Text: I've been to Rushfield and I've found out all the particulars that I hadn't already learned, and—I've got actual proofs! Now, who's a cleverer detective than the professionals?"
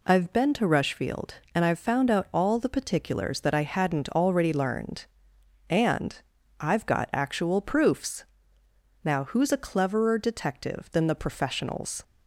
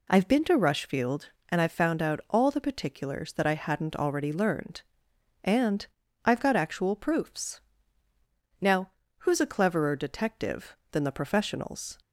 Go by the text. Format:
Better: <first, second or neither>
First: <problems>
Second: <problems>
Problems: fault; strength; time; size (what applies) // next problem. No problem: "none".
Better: neither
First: none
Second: none